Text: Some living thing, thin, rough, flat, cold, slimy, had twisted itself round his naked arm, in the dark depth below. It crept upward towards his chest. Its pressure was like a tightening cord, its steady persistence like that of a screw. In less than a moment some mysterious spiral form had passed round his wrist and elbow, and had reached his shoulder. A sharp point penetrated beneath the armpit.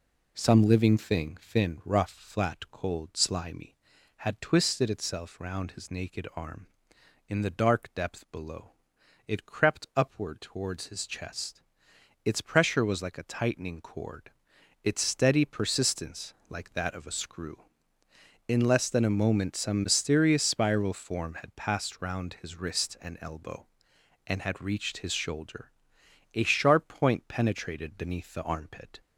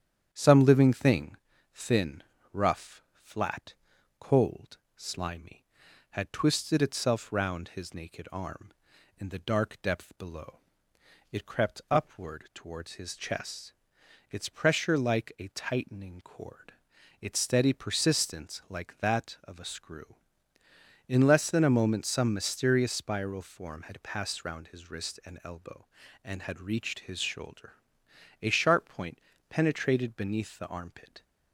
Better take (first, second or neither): first